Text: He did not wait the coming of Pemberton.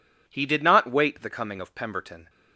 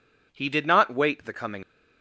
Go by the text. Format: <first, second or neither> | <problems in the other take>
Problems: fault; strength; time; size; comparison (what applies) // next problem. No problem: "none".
first | stops before "of Pemberton"; at 1.6 s